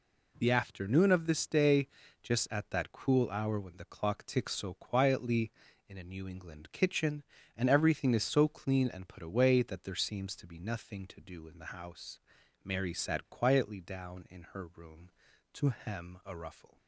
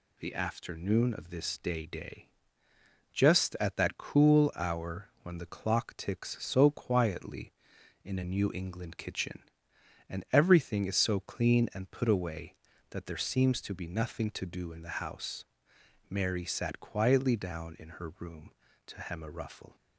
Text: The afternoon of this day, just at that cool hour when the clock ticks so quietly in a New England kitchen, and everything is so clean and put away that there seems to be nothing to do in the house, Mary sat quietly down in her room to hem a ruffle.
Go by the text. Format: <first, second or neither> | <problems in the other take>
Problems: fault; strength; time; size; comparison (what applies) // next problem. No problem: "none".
first | says "day" twice; at 1.9 s